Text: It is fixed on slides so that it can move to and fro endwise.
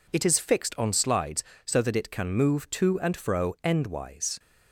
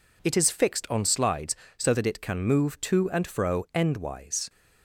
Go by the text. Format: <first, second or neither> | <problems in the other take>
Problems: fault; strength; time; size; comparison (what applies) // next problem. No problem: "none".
neither | none